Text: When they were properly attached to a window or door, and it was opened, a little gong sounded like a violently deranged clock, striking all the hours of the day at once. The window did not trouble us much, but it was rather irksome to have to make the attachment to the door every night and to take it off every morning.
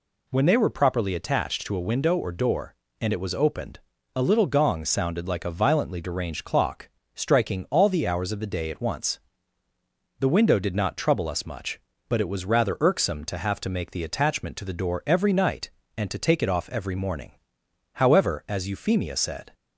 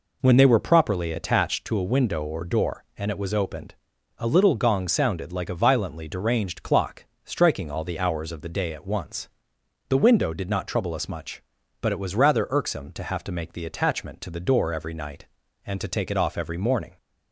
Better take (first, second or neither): second